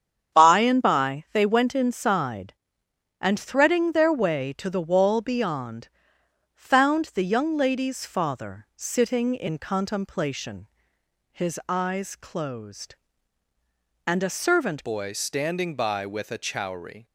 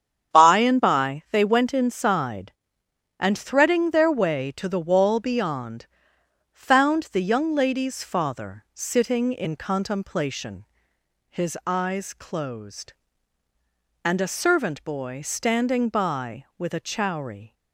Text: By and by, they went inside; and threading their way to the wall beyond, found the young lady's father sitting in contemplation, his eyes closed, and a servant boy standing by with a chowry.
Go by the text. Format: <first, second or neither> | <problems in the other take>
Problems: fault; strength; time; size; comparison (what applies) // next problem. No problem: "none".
second | starts louder than the rest; strong; until 1.4 s; 8.5 dB; strong in the second // changes voice at "boy"; from 14.8 s on; 2.2 s long